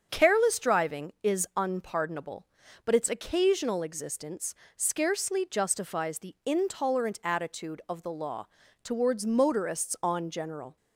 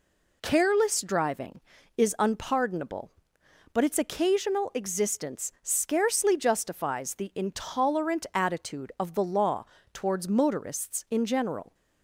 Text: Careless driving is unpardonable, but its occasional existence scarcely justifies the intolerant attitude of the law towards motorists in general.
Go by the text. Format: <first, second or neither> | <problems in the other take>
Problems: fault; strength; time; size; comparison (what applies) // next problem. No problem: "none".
second | starts louder than the rest; until 1.1 s; 7 dB // pauses between "existence" and "scarcely"; slight; at 4.5 s; 0.20 s long // pauses between "law" and "towards"; slight; at 8.4 s; 0.36 s long; slight in the second // says "on" for "in"; at 10.0 s